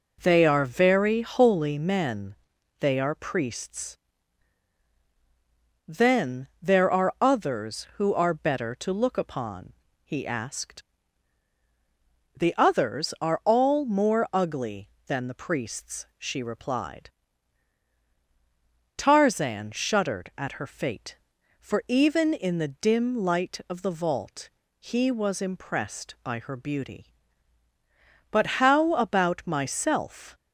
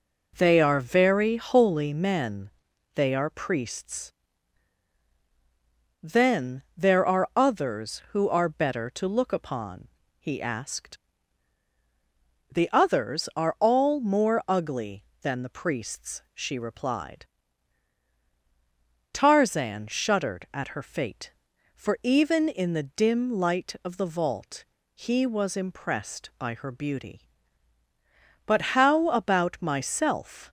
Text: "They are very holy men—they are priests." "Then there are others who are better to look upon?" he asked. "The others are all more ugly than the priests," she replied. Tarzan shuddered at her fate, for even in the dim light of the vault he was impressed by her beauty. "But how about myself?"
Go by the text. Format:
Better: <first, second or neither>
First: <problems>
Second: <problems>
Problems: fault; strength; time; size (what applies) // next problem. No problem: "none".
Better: neither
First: pauses between "vault" and "he"; slight; at 24.4 s; 0.32 s long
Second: pauses between "vault" and "he"; slight; at 24.6 s; 0.32 s long